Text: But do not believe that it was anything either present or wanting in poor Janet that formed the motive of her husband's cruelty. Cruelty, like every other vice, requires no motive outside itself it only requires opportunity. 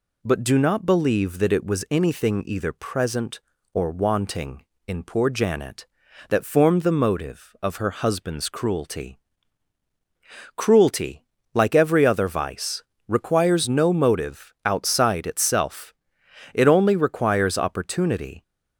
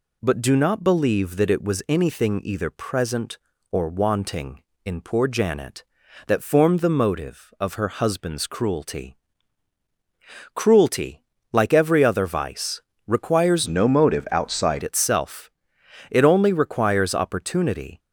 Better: first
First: pauses between "itself" and "it"; noticeable; at 15.9 s; 0.60 s long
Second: changes voice from "no" to "outside"; from 13.6 to 14.8 s; 1.2 s long // pauses between "itself" and "it"; noticeable; at 15.5 s; 0.60 s long

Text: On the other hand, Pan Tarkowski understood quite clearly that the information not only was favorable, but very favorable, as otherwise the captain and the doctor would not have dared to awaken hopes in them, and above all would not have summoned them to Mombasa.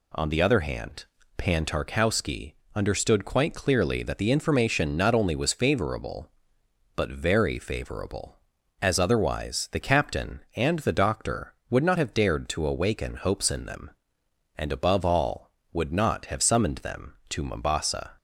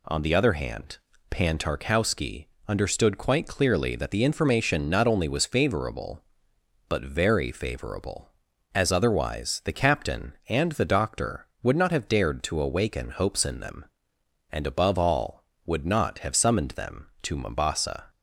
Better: neither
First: pauses between "Tarkowski" and "understood"; slight; at 2.5 s; 0.20 s long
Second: pauses between "Tarkowski" and "understood"; slight; at 2.4 s; 0.20 s long

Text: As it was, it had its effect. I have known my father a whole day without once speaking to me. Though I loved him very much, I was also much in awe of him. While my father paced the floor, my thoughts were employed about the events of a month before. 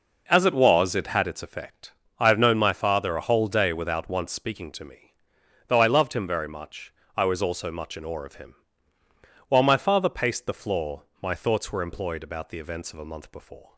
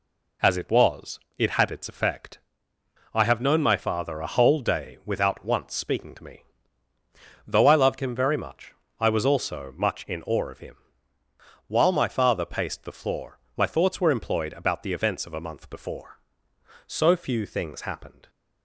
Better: first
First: none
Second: goes on to say "So few things happened"; from 16.8 s on; 1.4 s long

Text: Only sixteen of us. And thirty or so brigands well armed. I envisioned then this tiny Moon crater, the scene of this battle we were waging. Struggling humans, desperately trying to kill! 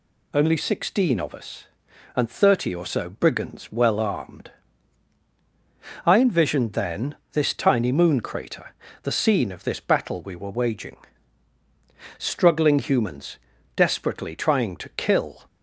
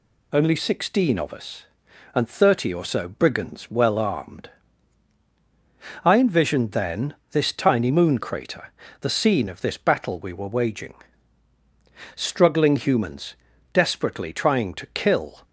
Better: neither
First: pauses between "then" and "this"; slight; at 7.1 s; 0.18 s long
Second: pauses between "then" and "this"; slight; at 7.1 s; 0.18 s long

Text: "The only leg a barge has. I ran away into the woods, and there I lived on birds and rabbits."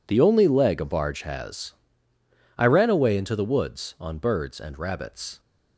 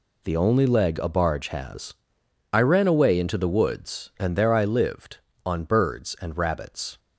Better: second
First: skips "and there I lived"; at 3.9 s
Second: none

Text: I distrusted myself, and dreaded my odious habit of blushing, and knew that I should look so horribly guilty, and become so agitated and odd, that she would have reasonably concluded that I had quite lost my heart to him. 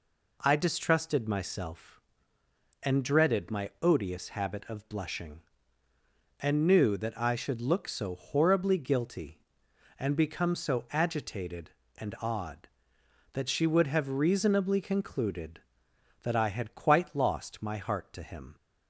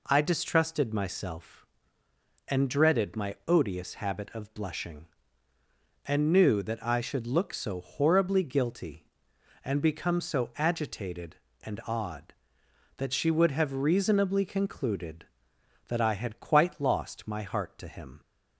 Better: neither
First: none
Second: none

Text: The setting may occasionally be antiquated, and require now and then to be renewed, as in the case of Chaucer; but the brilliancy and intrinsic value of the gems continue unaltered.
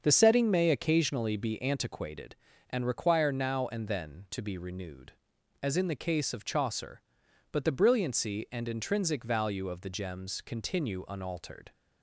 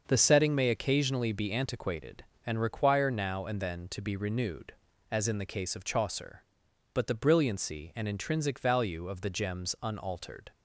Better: first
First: starts louder than the rest; until 1.0 s; 6.5 dB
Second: starts louder than the rest; until 1.0 s; 6.5 dB // skips "continue"; at 9.7 s

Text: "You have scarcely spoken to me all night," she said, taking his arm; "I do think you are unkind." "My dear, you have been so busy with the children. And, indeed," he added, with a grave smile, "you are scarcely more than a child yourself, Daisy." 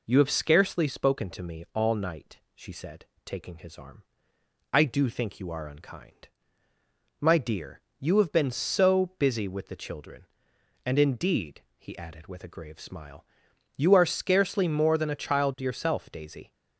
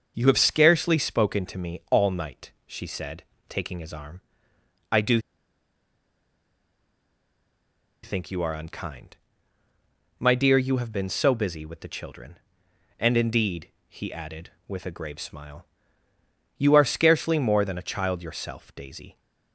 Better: first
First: none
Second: starts louder than the rest; until 1.1 s; 6 dB // pauses between "do" and "think"; strong; at 5.1 s; 2.8 s long

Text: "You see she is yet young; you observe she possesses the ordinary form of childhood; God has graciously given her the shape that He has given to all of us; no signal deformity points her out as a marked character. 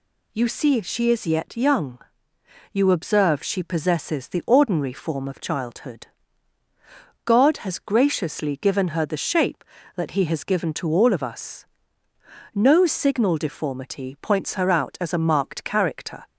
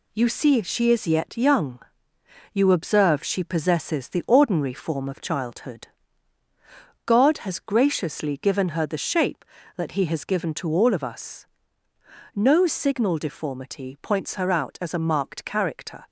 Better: first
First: none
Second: gets quieter; noticeable; throughout; 5 dB

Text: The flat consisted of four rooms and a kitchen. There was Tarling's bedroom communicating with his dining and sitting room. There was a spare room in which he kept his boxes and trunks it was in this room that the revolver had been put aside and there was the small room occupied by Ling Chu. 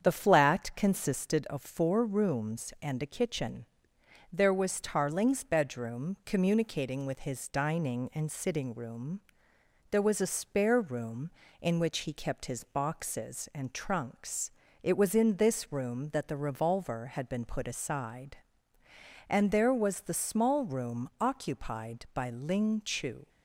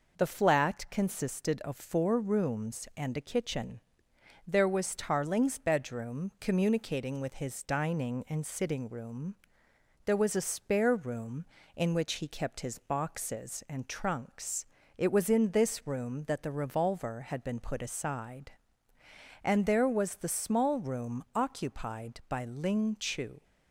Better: second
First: starts louder than the rest; strong; until 1.4 s; 7.5 dB // pauses between "trunks" and "it"; slight; at 14.5 s; 0.30 s long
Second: pauses between "trunks" and "it"; slight; at 14.6 s; 0.30 s long

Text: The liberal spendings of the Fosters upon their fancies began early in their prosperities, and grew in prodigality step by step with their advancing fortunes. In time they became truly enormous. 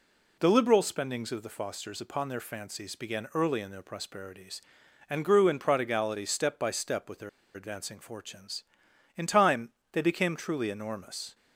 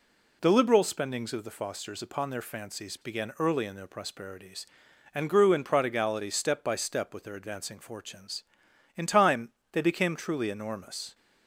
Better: second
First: pauses between "their" and "advancing"; slight; at 7.2 s; 0.25 s long // pauses between "time" and "they"; slight; at 9.7 s; 0.20 s long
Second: pauses between "time" and "they"; slight; at 9.5 s; 0.20 s long

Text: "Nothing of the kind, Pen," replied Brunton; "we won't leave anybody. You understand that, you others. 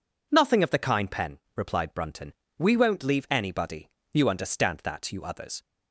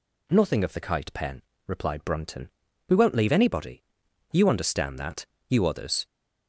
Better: first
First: none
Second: says "kite" for "kind"; at 0.7 s

